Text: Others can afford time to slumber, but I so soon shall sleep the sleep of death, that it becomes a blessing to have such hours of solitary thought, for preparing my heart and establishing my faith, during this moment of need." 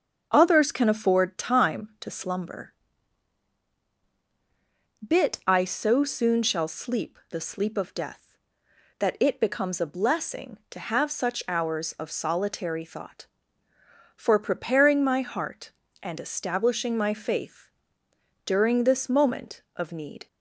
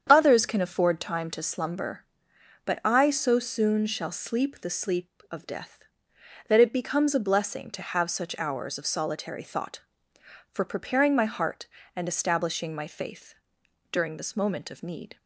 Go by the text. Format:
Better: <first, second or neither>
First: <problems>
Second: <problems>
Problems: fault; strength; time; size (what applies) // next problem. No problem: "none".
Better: second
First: starts louder than the rest; until 1.3 s; 7 dB // says "bit" for "but"; at 5.0 s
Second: starts louder than the rest; strong; until 1.1 s; 8 dB